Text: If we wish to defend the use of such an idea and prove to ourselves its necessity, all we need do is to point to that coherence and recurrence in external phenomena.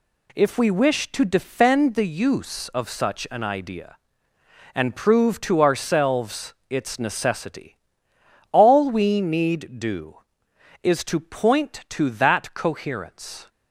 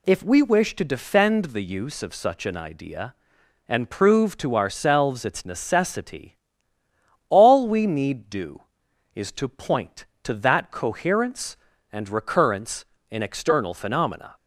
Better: second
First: pauses between "ourselves" and "its"; slight; at 6.5 s; 0.16 s long // stops before "and recurrence in external phenomena"; at 13.4 s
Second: none

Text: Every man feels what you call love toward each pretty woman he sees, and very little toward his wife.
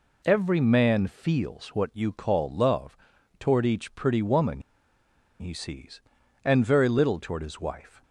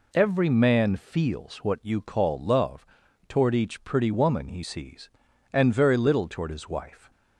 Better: second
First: pauses between "love" and "toward"; at 2.9 s; 0.44 s long // pauses between "woman" and "he"; noticeable; at 4.6 s; 0.79 s long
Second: pauses between "love" and "toward"; at 2.8 s; 0.44 s long

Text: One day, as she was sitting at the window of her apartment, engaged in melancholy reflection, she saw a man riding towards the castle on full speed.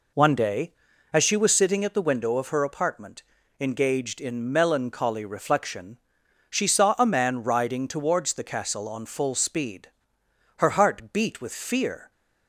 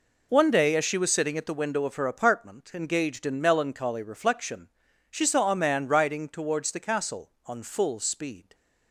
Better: second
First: goes on to say "Her heart beat with fear"; from 10.5 s on; 1.5 s long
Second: none

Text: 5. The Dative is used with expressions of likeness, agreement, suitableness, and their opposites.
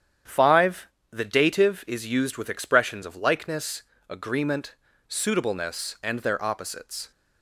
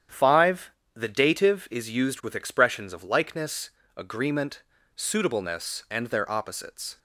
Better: neither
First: starts louder than the rest; strong; until 1.4 s; 9.5 dB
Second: starts louder than the rest; strong; until 1.3 s; 9.5 dB

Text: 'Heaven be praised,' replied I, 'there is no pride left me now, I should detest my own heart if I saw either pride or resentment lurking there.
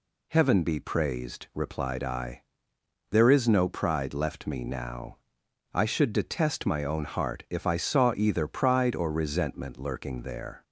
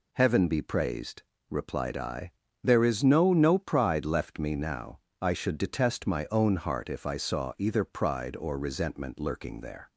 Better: first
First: none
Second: says "no" twice; at 3.3 s

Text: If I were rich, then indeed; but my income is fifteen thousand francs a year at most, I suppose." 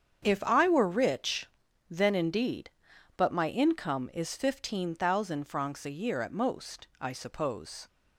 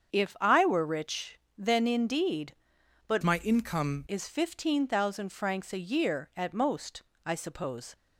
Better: first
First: starts louder than the rest; strong; until 1.2 s; 7.5 dB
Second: starts louder than the rest; strong; until 1.1 s; 7.5 dB // changes voice from "my" to "income"; from 3.2 to 4.0 s; 0.8 s long

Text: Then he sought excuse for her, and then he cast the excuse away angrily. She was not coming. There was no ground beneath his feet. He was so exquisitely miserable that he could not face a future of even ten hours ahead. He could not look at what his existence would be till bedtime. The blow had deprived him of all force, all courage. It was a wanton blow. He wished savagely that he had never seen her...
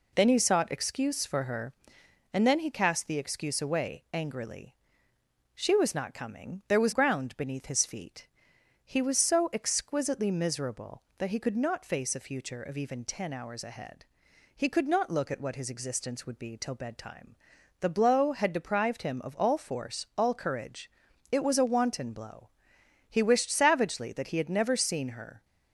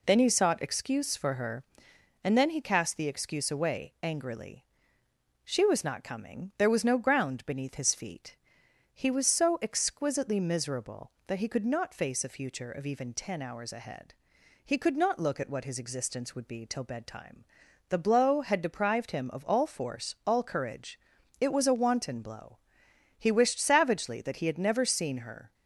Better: second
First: skips "no"; at 6.9 s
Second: none

